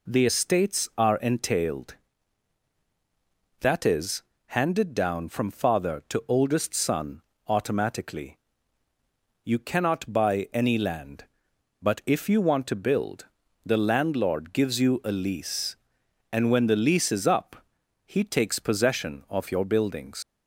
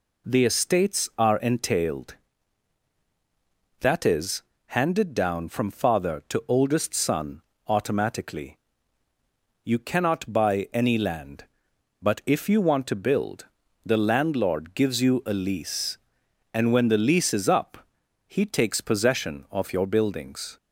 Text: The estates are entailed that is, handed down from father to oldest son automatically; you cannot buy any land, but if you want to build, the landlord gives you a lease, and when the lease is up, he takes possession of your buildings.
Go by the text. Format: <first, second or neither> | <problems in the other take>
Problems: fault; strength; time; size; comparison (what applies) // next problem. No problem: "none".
second | pauses between "son" and "automatically"; slight; at 7.2 s; 0.24 s long; slight in the second // leaves "buildings" unfinished; at 20.2 s; 125 ms